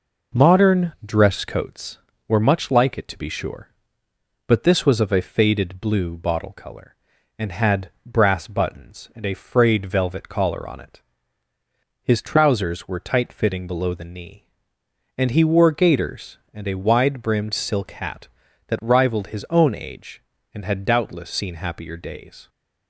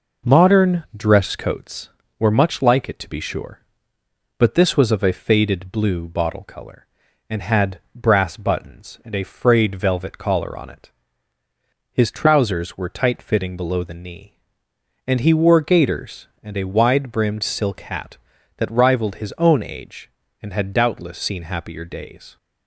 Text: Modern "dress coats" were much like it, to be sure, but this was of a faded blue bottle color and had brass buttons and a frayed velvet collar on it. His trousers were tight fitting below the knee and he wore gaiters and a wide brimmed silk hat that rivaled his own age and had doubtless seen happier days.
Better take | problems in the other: neither | none

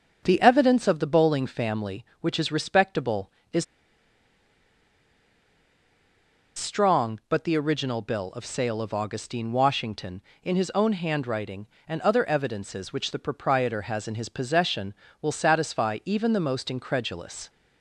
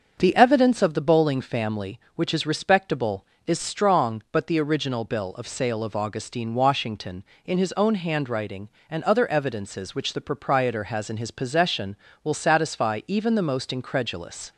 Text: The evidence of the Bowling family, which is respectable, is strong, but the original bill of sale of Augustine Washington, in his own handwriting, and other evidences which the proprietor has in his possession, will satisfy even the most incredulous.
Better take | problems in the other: second | starts louder than the rest; until 1.2 s; 6.5 dB; also in the second // pauses between "is" and "strong"; strong; at 3.6 s; 2.9 s long

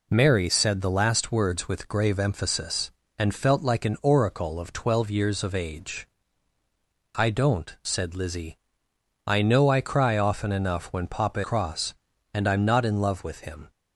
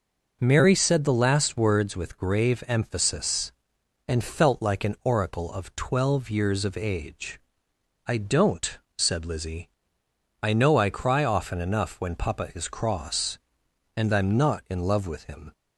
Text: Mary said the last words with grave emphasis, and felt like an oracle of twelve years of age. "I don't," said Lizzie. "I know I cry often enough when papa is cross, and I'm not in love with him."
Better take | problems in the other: second | skips "is"; at 11.4 s

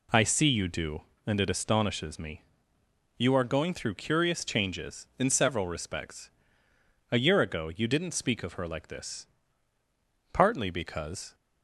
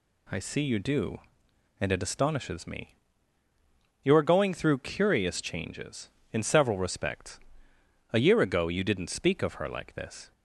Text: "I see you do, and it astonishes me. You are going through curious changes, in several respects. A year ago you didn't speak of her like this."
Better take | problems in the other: second | goes on to say "Partly because"; noticeable; from 10.3 s on; 1.0 s long

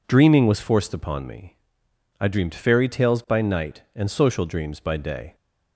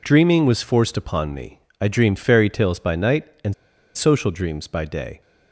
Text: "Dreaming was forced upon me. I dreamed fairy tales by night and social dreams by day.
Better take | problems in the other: first | pauses between "and" and "social"; at 3.5 s; 0.42 s long

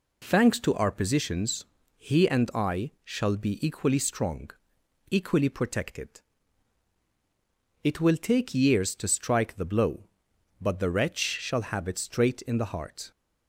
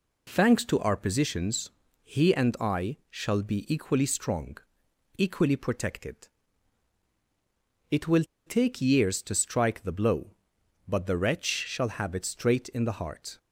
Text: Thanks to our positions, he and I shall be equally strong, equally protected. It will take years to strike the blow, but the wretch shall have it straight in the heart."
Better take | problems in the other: first | pauses between "will" and "take"; slight; at 8.2 s; 0.22 s long

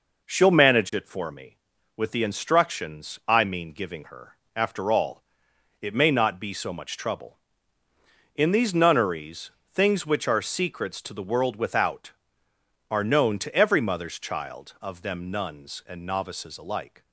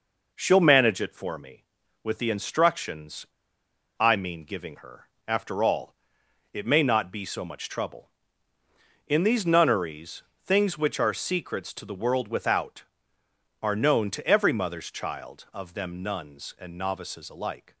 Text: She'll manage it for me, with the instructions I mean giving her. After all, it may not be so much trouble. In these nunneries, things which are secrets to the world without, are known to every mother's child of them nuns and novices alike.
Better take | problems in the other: first | pauses between "instructions" and "I"; noticeable; at 3.2 s; 0.73 s long

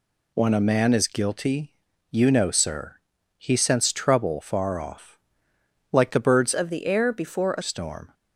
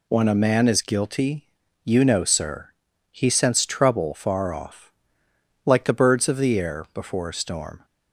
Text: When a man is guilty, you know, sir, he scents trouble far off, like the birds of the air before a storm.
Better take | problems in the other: second | changes voice from "of" to "a"; from 6.5 to 7.6 s; 1.1 s long

